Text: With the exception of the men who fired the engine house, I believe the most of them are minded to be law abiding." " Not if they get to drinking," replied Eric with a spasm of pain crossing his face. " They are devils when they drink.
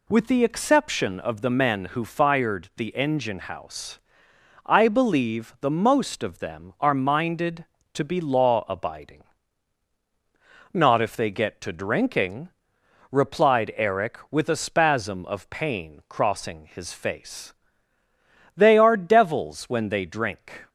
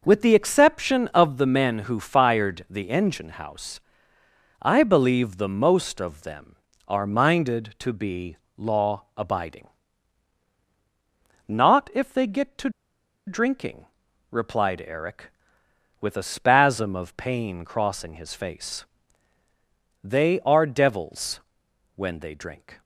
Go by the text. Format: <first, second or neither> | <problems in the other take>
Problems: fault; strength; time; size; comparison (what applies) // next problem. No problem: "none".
first | pauses between "be" and "law"; slight; at 8.3 s; 0.22 s long // pauses between "to" and "drinking"; noticeable; at 12.6 s; 0.57 s long // pauses between "devils" and "when"; noticeable; at 21.3 s; 0.56 s long